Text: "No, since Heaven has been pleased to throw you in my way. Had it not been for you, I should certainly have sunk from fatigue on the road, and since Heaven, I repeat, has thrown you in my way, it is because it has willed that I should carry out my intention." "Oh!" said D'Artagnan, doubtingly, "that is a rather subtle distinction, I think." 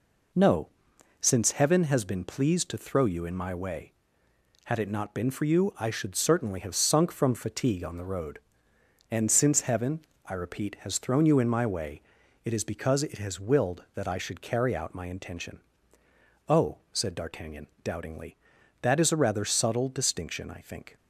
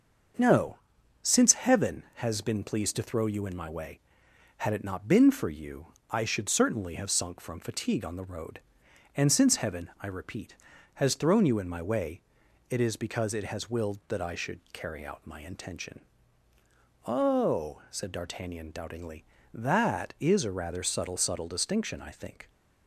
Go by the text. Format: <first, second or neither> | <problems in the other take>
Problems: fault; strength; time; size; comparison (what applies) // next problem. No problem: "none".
first | starts louder than the rest; until 1.8 s; 6.5 dB // says "subtle" twice; at 21.1 s